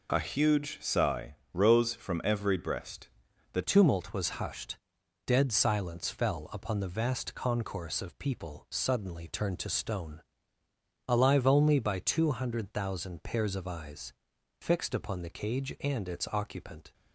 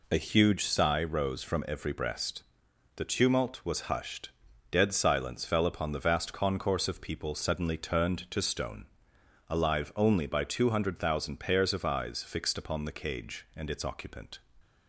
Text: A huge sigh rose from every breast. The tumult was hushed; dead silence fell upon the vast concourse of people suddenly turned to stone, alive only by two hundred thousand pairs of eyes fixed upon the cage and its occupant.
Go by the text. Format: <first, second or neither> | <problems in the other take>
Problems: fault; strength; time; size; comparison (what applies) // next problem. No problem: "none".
second | pauses between "sigh" and "rose"; slight; at 1.3 s; 0.18 s long // changes voice at "tumult"; from 3.6 s on; 13.3 s long // pauses between "eyes" and "fixed"; noticeable; at 14.1 s; 0.48 s long